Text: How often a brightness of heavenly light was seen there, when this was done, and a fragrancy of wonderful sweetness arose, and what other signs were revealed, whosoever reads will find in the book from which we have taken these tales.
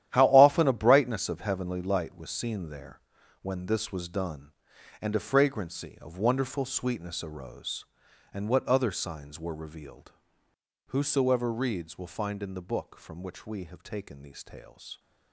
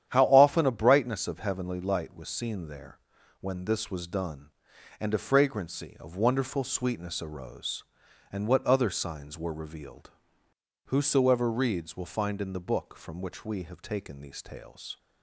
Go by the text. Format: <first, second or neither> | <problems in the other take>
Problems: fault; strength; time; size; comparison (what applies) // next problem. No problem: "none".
second | gets quieter; strong; throughout; 12 dB // starts louder than the rest; strong; until 1.1 s; 11.5 dB; strong in the second